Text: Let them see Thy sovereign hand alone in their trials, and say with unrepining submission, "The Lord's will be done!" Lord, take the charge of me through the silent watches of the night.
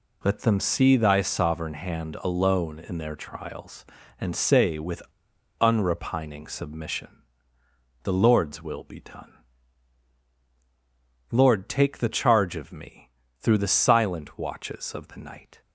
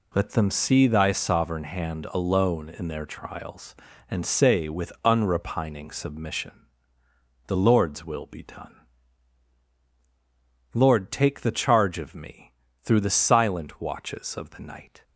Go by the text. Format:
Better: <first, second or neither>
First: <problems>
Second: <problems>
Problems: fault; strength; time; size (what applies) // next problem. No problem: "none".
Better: second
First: pauses between "with" and "unrepining"; noticeable; at 5.0 s; 0.58 s long // pauses between "me" and "through"; slight; at 13.1 s; 0.28 s long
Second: pauses between "me" and "through"; slight; at 12.5 s; 0.28 s long